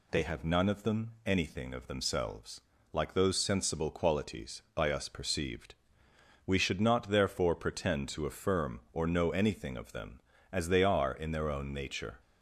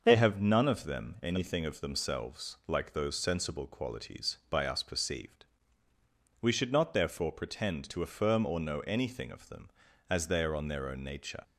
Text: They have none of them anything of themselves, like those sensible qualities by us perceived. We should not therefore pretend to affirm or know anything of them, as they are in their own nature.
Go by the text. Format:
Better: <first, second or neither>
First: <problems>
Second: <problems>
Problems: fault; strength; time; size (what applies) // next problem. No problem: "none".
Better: first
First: none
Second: starts louder than the rest; until 1.0 s; 6 dB // says "on" for "in"; at 10.5 s